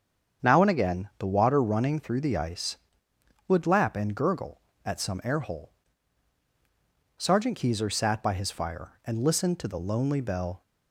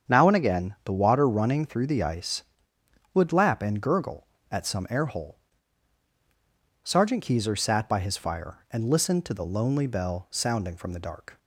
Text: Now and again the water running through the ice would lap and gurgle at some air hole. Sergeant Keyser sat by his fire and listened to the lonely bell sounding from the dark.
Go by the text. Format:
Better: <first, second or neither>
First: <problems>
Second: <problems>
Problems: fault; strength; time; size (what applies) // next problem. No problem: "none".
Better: second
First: starts louder than the rest; strong; until 1.5 s; 7.5 dB // stops before "sounding from the dark"; at 10.6 s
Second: starts louder than the rest; strong; until 1.1 s; 7.5 dB